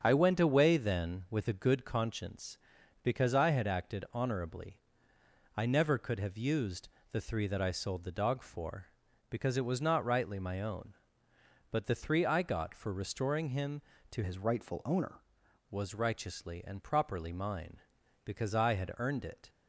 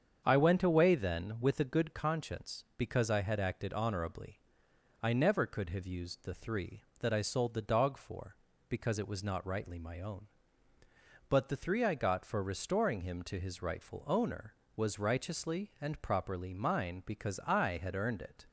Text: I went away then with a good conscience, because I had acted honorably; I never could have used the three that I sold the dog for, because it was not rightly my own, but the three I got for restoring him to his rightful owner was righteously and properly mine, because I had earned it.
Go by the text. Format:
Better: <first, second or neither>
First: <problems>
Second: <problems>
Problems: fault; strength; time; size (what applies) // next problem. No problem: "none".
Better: second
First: starts louder than the rest; strong; until 1.0 s; 7.5 dB // pauses between "used" and "the"; slight; at 6.8 s; 0.24 s long // changes voice from "his" to "owner"; from 14.2 to 15.2 s; 1.0 s long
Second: starts louder than the rest; strong; until 1.2 s; 7.5 dB